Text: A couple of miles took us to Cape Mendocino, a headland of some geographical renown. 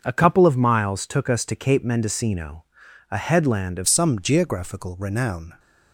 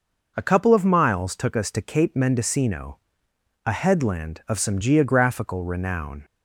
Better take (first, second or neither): second